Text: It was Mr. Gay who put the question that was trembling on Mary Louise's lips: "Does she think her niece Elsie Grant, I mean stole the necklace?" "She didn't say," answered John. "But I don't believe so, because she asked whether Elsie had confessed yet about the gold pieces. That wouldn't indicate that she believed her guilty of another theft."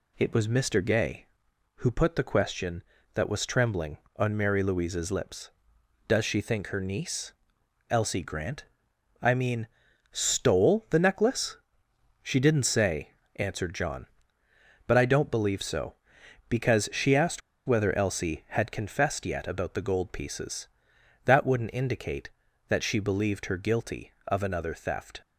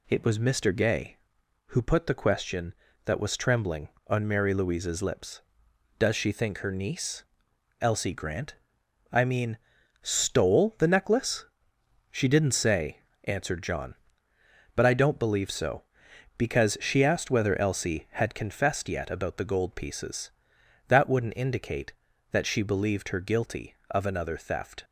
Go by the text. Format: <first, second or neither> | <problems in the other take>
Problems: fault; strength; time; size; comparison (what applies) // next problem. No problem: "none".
second | pauses between "niece" and "Elsie"; noticeable; at 7.3 s; 0.58 s long; noticeable in the second // pauses between "mean" and "stole"; at 9.6 s; 0.44 s long; also in the second // pauses between "asked" and "whether"; slight; at 17.4 s; 0.26 s long